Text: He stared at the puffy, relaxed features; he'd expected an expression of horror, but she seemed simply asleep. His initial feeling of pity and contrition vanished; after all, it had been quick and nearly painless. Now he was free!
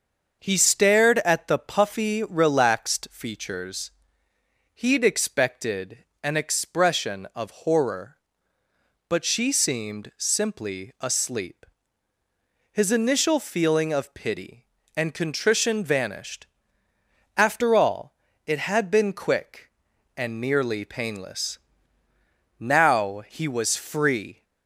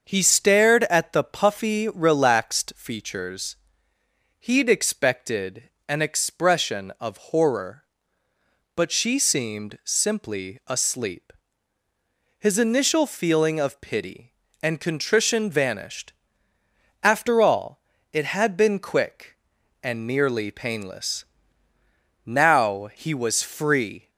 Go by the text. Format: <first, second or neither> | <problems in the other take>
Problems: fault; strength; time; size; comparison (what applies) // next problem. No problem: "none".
neither | starts louder than the rest; the same in both // pauses between "expected" and "an"; slight; the same in both